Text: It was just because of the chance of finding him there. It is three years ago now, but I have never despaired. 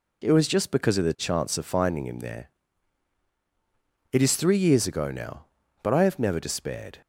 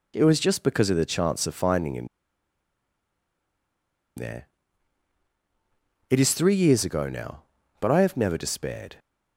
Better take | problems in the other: first | pauses between "him" and "there"; strong; at 2.0 s; 2.0 s long

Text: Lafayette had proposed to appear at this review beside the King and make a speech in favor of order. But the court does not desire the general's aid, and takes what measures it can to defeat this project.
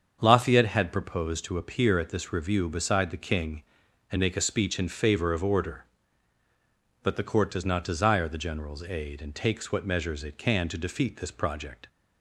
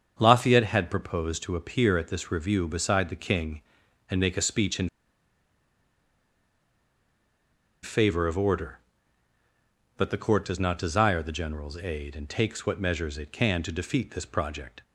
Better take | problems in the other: first | starts louder than the rest; until 1.1 s; 7 dB; also in the first // pauses between "in" and "favor"; strong; at 4.8 s; 2.9 s long

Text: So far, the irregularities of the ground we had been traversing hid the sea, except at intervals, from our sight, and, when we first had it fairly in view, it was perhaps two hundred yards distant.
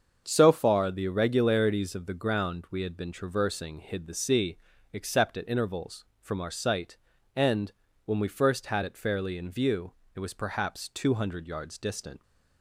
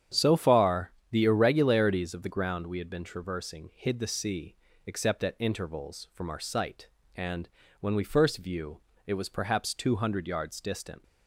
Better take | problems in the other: first | starts louder than the rest; strong; until 1.3 s; 9 dB; also in the first // skips "had it fairly in"; at 8.3 s

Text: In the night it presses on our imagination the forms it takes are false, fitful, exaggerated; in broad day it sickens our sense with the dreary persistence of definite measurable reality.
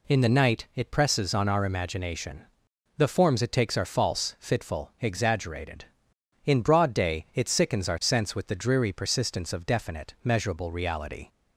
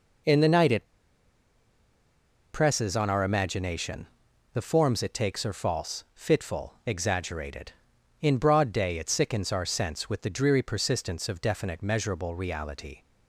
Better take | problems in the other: first | pauses between "it" and "presses"; strong; at 0.8 s; 1.6 s long // pauses between "imagination" and "the"; noticeable; at 4.0 s; 0.46 s long; noticeable in the first

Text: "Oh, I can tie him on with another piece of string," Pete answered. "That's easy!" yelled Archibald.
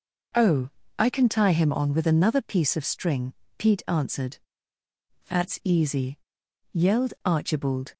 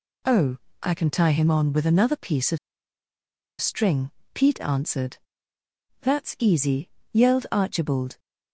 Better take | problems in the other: first | pauses between "of" and "string"; at 2.5 s; 1.0 s long

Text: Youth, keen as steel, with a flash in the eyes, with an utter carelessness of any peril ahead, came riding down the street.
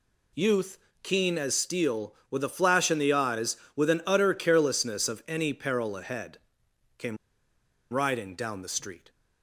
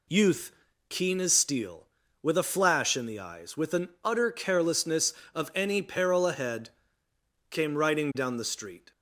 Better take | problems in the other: second | pauses between "came" and "riding"; noticeable; at 7.1 s; 0.75 s long

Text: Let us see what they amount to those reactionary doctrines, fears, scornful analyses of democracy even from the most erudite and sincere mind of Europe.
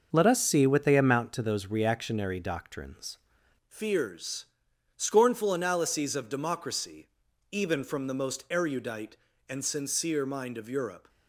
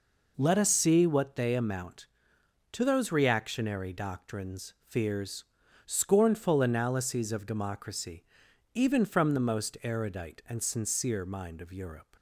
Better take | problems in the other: second | starts louder than the rest; noticeable; until 1.1 s; 6 dB // changes voice at "fears"; from 3.6 s on; 7.4 s long // pauses between "democracy" and "even"; at 7.0 s; 0.42 s long; noticeable in the second

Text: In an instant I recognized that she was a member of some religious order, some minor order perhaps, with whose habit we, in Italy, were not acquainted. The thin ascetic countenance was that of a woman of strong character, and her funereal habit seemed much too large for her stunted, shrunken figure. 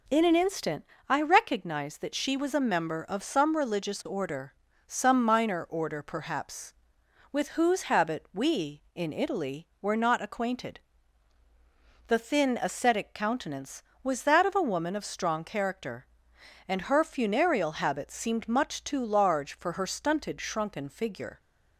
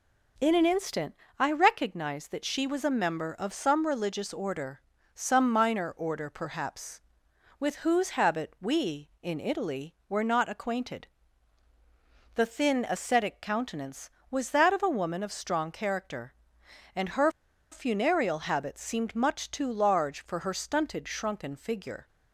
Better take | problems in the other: first | pauses between "instant" and "I"; slight; at 1.1 s; 0.24 s long; slight in the first // pauses between "her" and "funereal"; at 17.3 s; 0.40 s long

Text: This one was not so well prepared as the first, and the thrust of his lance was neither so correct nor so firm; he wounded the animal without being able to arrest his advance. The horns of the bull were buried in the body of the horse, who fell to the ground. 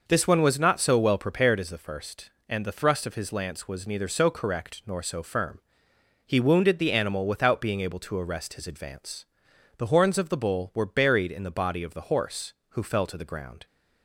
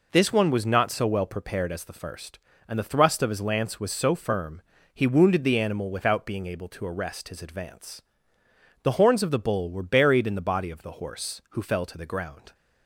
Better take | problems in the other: first | skips "neither so correct nor"; at 3.9 s

